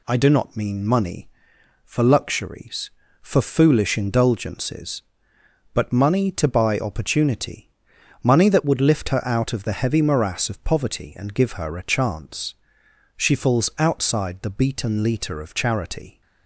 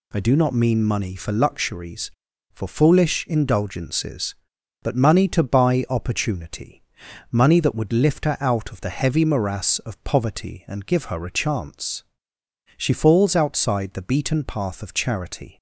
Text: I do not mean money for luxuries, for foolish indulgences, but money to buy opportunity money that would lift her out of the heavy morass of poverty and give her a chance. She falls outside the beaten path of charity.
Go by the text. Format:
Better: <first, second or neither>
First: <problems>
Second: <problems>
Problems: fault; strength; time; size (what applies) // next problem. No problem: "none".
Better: second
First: pauses between "opportunity" and "money"; noticeable; at 7.6 s; 0.56 s long // says "litre" for "path"; at 15.0 s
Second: pauses between "opportunity" and "money"; noticeable; at 6.7 s; 0.52 s long